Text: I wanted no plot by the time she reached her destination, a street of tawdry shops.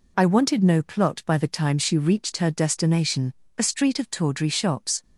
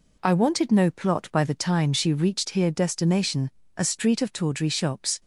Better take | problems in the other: first | says "here" for "her"; at 2.5 s

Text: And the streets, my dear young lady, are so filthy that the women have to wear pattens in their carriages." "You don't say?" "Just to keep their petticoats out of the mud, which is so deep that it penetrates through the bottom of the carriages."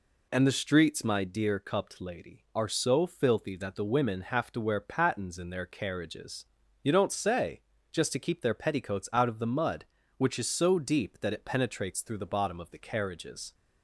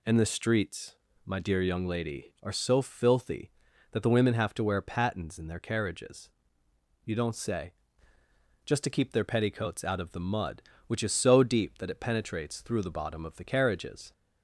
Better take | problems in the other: second | says "cupped" for "young"; at 1.5 s

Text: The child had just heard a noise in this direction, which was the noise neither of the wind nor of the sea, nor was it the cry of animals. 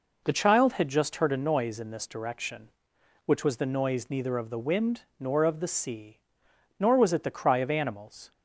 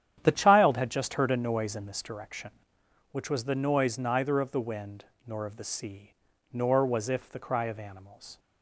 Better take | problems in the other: first | starts louder than the rest; strong; until 1.2 s; 10 dB // pauses between "wind" and "nor"; slight; at 5.0 s; 0.20 s long; slight in the first // says "if" for "it"; at 7.0 s

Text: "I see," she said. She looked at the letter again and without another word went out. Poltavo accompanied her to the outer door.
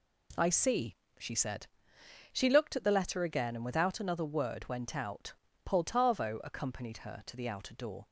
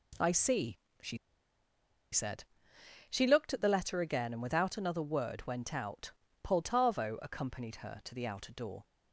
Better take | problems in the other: first | pauses between "she" and "said"; noticeable; at 1.1 s; 0.94 s long

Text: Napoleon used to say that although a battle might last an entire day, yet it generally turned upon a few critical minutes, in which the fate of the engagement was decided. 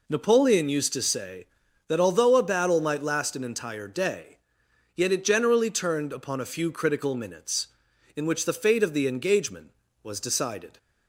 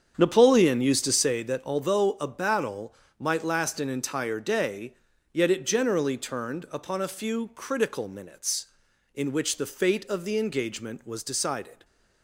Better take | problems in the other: first | starts louder than the rest; strong; until 1.4 s; 7.5 dB // pauses between "battle" and "might"; slight; at 2.9 s; 0.24 s long

